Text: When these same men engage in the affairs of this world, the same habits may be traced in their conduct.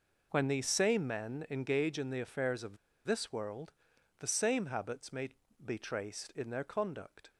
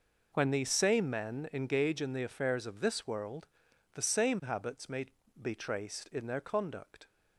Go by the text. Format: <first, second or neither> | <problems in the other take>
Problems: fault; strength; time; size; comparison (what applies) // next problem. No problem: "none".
second | pauses between "of" and "this"; slight; at 2.7 s; 0.29 s long // pauses between "may" and "be"; slight; at 5.2 s; 0.36 s long; slight in the second